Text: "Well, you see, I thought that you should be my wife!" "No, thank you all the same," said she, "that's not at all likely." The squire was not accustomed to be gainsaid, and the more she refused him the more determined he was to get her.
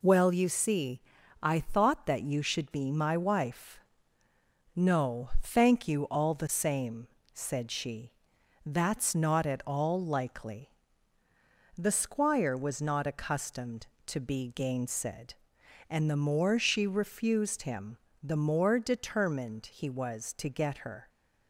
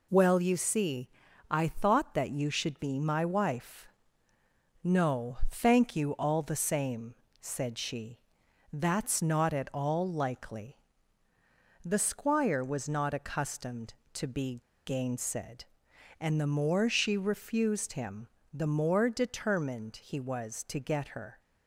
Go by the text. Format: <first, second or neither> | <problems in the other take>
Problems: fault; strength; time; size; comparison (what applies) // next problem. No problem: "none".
first | pauses between "be" and "gainsaid"; slight; at 14.5 s; 0.27 s long // pauses between "him" and "the"; slight; at 18.2 s; 0.28 s long; slight in the first